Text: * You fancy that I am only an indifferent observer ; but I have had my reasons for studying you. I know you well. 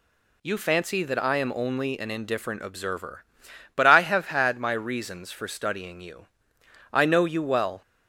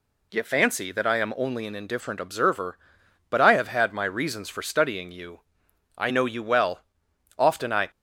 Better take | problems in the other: first | goes on to say "Often I"; from 7.3 s on; 0.54 s long

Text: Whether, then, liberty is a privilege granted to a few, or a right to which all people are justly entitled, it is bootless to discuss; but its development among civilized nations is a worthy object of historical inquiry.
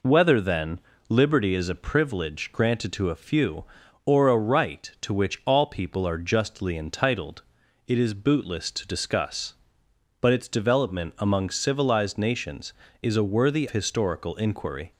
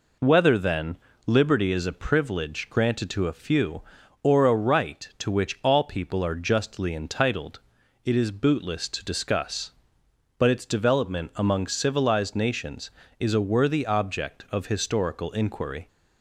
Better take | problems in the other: second | skips "object of"; at 13.6 s

